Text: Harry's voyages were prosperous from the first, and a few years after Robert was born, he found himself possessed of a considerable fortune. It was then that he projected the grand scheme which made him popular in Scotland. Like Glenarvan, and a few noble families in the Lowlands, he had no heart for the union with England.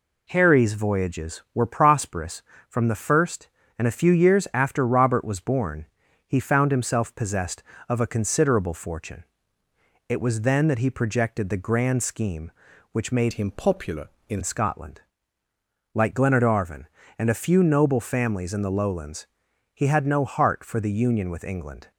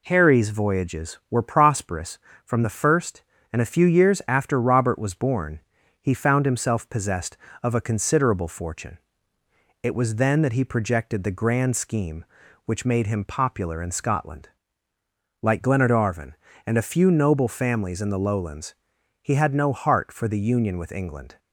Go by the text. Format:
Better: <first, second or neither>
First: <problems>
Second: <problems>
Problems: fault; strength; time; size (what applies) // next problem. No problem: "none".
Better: second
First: changes voice from "him" to "in"; from 13.3 to 14.4 s; 1.1 s long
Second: none